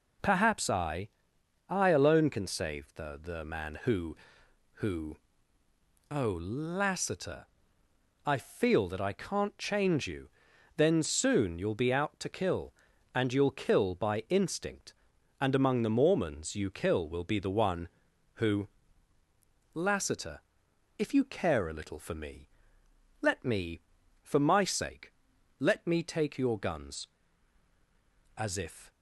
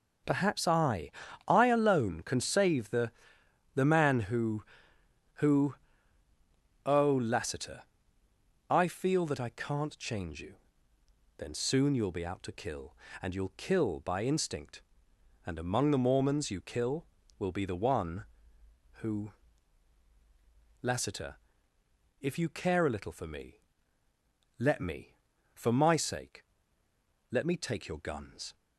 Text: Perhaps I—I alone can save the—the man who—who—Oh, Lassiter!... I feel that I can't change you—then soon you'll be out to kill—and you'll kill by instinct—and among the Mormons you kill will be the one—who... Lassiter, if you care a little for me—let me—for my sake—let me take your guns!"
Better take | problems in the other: second | goes on to say "As if"; from 28.3 s on; 0.54 s long

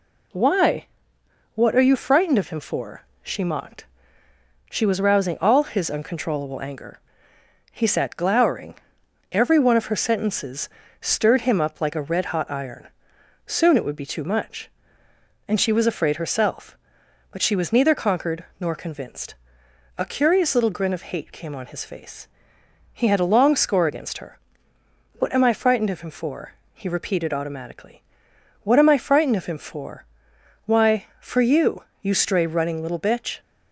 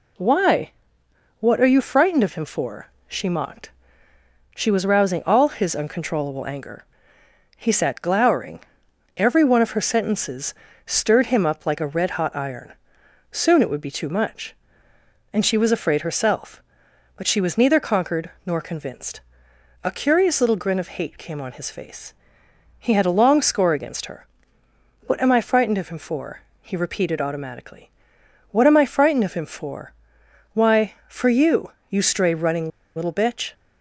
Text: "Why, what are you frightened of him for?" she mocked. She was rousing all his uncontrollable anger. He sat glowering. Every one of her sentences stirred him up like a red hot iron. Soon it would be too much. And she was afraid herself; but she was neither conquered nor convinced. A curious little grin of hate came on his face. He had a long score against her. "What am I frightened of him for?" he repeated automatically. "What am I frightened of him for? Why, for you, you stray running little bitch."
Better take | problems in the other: first | pauses between "sentences" and "stirred"; slight; at 10.5 s; 0.32 s long; slight in the first // pauses between "conquered" and "nor"; slight; at 18.2 s; 0.16 s long; slight in the first // pauses between "running" and "little"; slight; at 32.6 s; 0.26 s long

